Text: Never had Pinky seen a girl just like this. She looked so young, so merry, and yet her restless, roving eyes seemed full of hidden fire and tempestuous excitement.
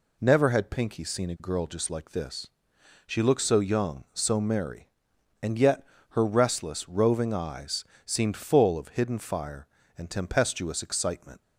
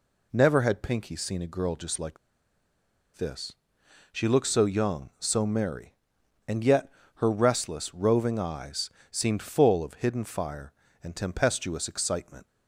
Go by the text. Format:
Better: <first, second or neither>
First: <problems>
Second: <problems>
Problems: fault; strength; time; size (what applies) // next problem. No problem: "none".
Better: first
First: pauses between "yet" and "her"; slight; at 5.8 s; 0.28 s long // pauses between "eyes" and "seemed"; slight; at 7.8 s; 0.22 s long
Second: pauses between "like" and "this"; at 2.1 s; 0.99 s long // pauses between "yet" and "her"; slight; at 6.8 s; 0.28 s long // pauses between "eyes" and "seemed"; slight; at 8.8 s; 0.22 s long